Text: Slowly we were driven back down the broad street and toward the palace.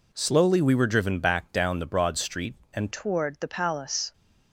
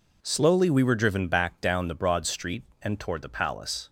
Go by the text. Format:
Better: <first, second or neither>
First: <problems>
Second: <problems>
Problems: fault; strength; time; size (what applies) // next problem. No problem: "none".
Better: second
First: changes voice at "toward"; from 2.9 s on; 1.2 s long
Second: none